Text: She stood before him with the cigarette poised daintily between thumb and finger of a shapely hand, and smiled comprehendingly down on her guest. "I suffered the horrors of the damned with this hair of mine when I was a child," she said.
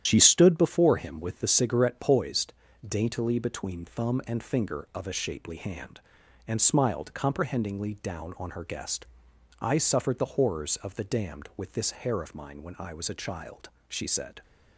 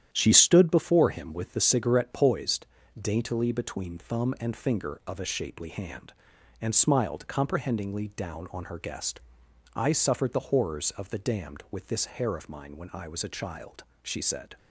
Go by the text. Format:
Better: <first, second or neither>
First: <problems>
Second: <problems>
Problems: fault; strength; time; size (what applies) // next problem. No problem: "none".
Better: second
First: loses the start of "She"; at 0.0 s; 50 ms // starts louder than the rest; strong; until 1.0 s; 10.5 dB // pauses between "poised" and "daintily"; slight; at 2.5 s; 0.34 s long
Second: starts louder than the rest; strong; until 1.1 s; 10.5 dB // pauses between "poised" and "daintily"; slight; at 2.6 s; 0.34 s long